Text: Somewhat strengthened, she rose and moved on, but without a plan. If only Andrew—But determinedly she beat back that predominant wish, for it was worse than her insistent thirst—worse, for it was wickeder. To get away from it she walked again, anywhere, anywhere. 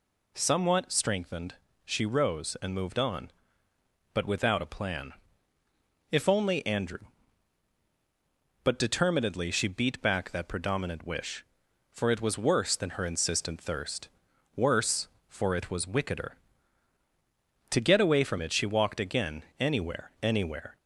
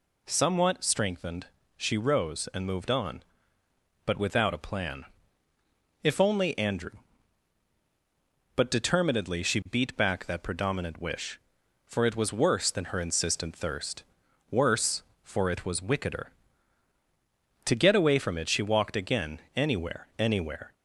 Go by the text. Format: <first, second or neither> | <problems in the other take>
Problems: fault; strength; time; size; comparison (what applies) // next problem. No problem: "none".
neither | none